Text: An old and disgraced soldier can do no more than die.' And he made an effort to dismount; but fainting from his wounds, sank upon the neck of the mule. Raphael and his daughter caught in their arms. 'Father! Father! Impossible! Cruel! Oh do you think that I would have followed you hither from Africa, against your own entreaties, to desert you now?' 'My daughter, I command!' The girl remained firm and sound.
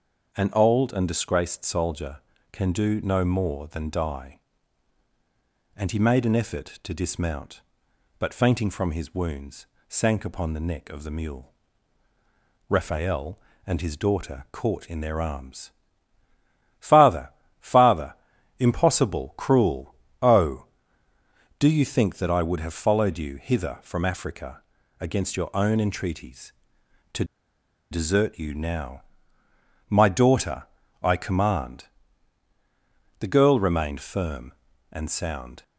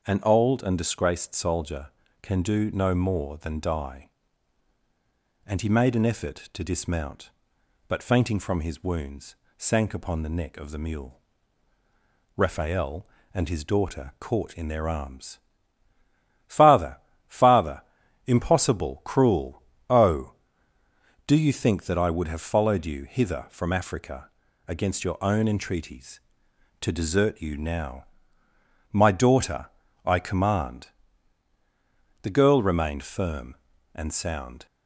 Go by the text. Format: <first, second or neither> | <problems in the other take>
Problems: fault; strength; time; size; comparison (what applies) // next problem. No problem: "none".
second | starts louder than the rest; until 1.3 s; 6.5 dB; also in the second // pauses between "to" and "desert"; noticeable; at 27.2 s; 0.67 s long